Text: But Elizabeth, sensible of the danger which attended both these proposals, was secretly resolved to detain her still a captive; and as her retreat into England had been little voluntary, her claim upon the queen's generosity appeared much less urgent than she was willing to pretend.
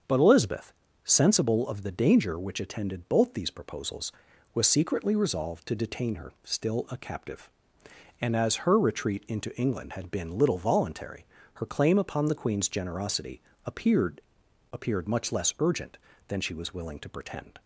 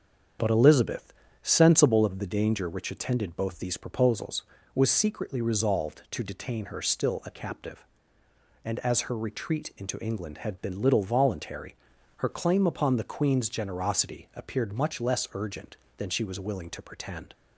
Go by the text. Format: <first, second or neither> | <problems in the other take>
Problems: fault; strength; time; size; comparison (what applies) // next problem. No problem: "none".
second | starts louder than the rest; until 1.3 s; 6.5 dB; strong in the second // pauses between "generosity" and "appeared"; slight; at 13.4 s; 0.22 s long // says "appeared" twice; at 14.7 s